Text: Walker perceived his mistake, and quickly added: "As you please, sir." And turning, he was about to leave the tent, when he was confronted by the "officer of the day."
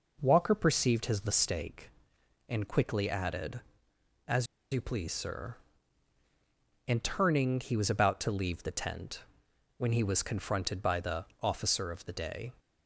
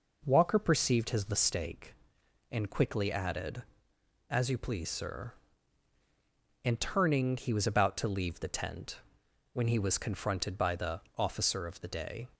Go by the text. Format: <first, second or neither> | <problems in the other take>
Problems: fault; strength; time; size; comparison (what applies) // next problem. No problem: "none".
second | pauses between "As" and "you"; slight; at 4.4 s; 0.28 s long // pauses between "the" and "officer"; slight; at 11.2 s; 0.16 s long; slight in the second